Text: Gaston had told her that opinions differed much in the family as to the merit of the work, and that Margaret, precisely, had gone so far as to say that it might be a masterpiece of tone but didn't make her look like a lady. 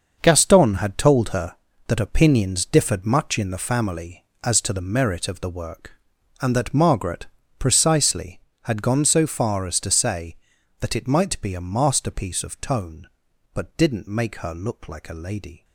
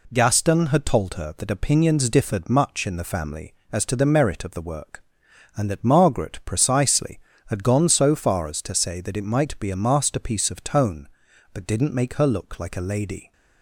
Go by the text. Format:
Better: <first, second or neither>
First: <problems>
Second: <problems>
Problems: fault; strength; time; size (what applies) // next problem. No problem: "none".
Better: second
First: gets quieter; strong; throughout; 11 dB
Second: none